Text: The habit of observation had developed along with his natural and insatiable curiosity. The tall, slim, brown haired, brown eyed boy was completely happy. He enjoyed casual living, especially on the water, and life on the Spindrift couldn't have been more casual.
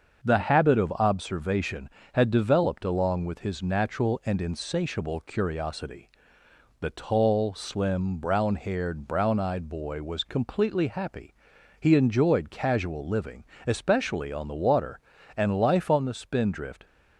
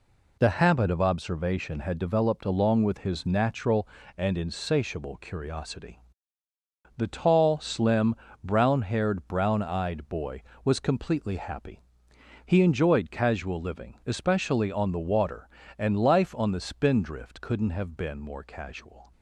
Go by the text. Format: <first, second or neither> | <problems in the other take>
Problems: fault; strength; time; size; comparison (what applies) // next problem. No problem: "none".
second | starts louder than the rest; until 1.3 s; 6.5 dB // stops before "couldn't have been more casual"; at 16.8 s